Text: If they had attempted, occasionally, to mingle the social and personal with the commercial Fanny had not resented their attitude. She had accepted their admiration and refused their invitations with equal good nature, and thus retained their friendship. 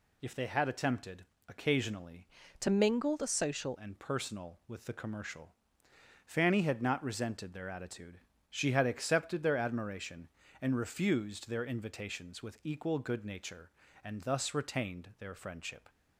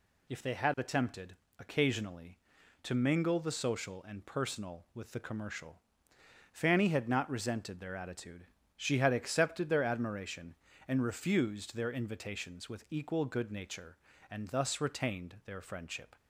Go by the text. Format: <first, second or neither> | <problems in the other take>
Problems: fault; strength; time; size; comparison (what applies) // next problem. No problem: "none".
second | changes voice from "to" to "social"; from 2.5 to 3.7 s; 1.2 s long // pauses between "commercial" and "Fanny"; noticeable; at 5.5 s; 0.72 s long; noticeable in the second